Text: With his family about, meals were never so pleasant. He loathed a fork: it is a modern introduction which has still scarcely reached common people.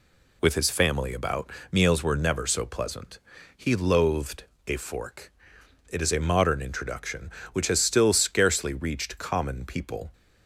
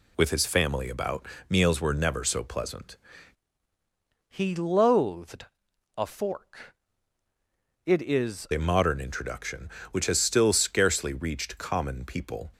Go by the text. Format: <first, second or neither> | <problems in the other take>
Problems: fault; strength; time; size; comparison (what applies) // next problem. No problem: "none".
first | changes voice from "He" to "is"; from 4.2 to 8.4 s; 4.2 s long // pauses between "loathed" and "a"; noticeable; at 5.4 s; 0.52 s long; slight in the first